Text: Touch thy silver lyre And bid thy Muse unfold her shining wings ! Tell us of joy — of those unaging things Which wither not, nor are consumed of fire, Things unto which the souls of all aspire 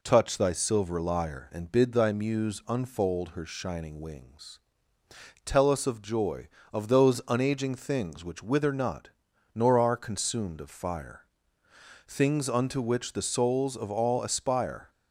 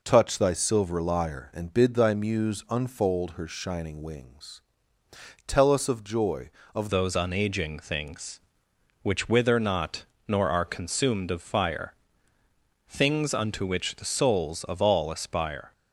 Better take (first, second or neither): first